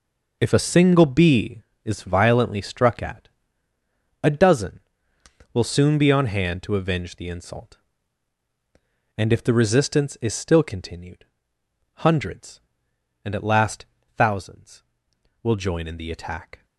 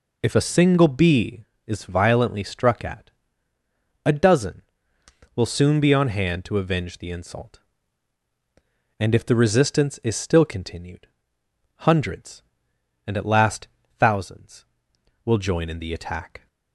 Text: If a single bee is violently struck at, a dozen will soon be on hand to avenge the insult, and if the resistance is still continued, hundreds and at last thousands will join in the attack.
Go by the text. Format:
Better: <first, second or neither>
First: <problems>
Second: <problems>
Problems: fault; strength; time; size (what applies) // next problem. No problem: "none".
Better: second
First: gets quieter; strong; throughout; 11 dB // pauses between "last" and "thousands"; slight; at 13.8 s; 0.32 s long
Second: pauses between "last" and "thousands"; slight; at 13.6 s; 0.32 s long